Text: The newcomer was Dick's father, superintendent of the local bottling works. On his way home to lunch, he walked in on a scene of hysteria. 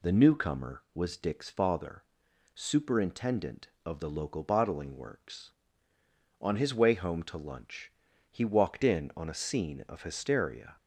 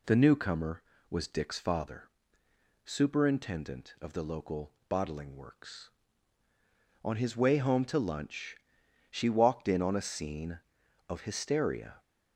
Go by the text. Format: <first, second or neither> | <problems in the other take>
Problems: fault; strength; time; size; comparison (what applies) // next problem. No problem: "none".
first | pauses between "local" and "bottling"; slight; at 4.7 s; 0.16 s long // says "she" for "he"; at 9.0 s